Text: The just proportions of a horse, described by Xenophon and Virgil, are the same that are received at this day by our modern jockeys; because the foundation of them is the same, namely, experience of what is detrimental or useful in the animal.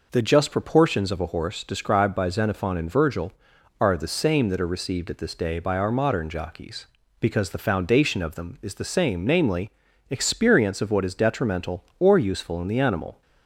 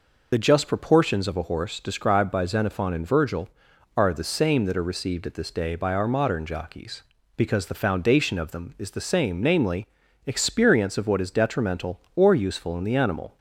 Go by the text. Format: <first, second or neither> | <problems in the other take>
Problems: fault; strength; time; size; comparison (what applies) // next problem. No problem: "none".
first | loses the start of "The"; at 0.3 s; 50 ms